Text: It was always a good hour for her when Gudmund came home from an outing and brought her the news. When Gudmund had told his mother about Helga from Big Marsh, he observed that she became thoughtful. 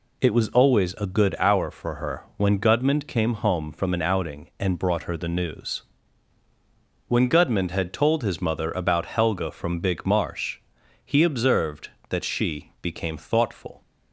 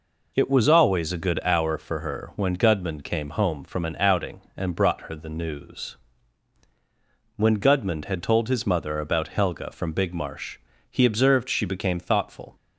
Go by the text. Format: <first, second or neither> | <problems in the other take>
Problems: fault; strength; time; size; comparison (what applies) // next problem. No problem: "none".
first | skips "that"; at 11.4 s